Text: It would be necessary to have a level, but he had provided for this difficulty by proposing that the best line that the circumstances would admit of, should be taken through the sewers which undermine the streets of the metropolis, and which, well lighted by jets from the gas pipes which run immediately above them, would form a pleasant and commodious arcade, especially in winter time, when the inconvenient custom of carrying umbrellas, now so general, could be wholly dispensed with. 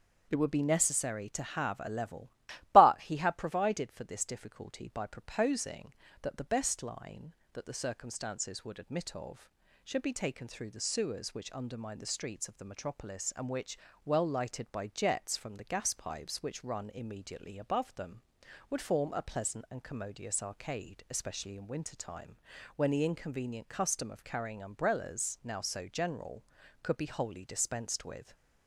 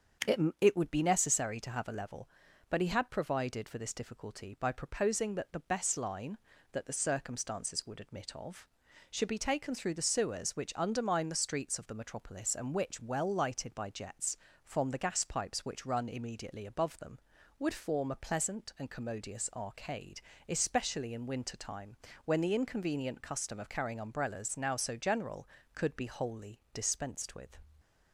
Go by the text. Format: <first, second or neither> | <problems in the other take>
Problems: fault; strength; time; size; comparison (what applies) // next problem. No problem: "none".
first | starts louder than the rest; until 1.4 s; 7 dB; also in the first // says "It" twice; at 0.5 s // pauses between "wholly" and "dispensed"; slight; at 26.5 s; 0.16 s long